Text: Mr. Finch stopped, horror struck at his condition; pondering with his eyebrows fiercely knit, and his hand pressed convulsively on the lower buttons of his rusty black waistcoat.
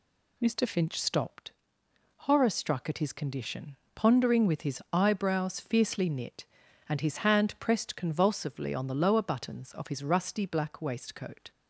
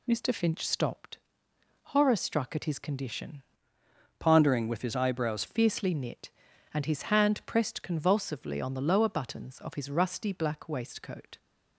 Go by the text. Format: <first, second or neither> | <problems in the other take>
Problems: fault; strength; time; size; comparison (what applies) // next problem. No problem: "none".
first | changes voice from "pondering" to "eyebrows"; from 4.1 to 5.4 s; 1.3 s long